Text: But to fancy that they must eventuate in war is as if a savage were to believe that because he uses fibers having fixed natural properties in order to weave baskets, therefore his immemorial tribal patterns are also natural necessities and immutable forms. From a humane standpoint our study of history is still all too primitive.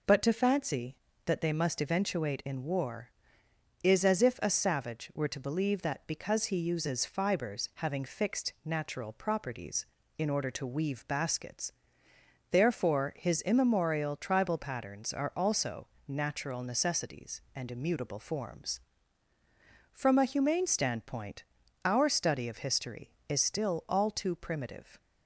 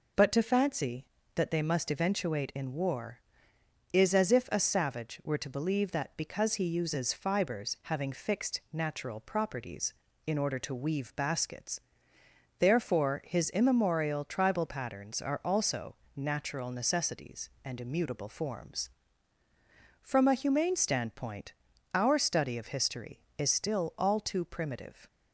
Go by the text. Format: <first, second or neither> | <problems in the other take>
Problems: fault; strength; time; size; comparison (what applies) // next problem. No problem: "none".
neither | pauses between "also" and "natural"; slight; the same in both // pauses between "standpoint" and "our"; the same in both